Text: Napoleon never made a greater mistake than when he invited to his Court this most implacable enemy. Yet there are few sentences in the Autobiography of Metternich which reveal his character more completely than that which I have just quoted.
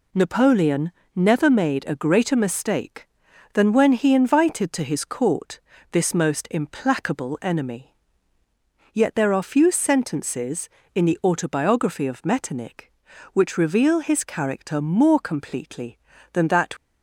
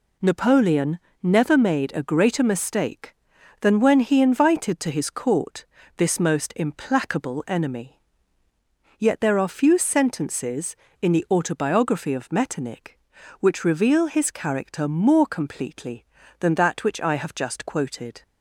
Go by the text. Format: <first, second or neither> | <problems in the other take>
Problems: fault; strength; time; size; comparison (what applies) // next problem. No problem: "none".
second | pauses between "Napoleon" and "never"; slight; at 0.9 s; 0.24 s long; slight in the second // pauses between "Court" and "this"; slight; at 5.6 s; 0.32 s long; slight in the second // stops before "which I have just quoted"; at 16.7 s